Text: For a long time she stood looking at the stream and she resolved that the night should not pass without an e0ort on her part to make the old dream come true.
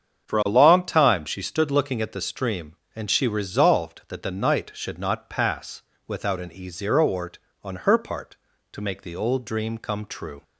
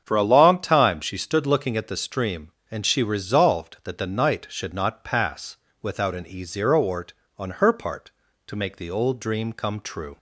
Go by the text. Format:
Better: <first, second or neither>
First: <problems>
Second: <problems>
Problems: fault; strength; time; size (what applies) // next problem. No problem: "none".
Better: neither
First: starts louder than the rest; strong; until 1.3 s; 7.5 dB // pauses between "pass" and "without"; slight; at 5.8 s; 0.26 s long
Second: starts louder than the rest; strong; until 1.0 s; 7.5 dB // pauses between "pass" and "without"; slight; at 5.5 s; 0.26 s long